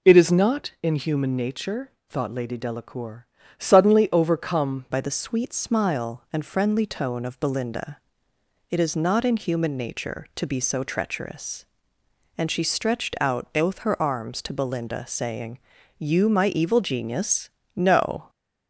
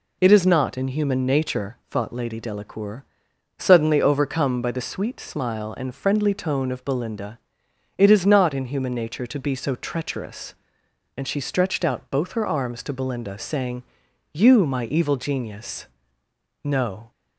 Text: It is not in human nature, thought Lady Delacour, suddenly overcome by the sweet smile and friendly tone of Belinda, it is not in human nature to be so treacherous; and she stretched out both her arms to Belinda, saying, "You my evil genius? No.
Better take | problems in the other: second | changes voice at "by"; from 4.9 s on; 13.3 s long

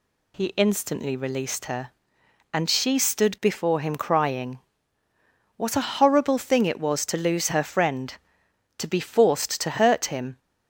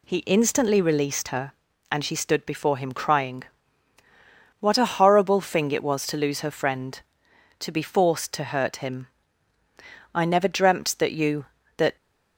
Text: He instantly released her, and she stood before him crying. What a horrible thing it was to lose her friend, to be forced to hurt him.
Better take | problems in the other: first | goes on to say "I never dreamt that you that"; strong; from 10.1 s on; 1.8 s long

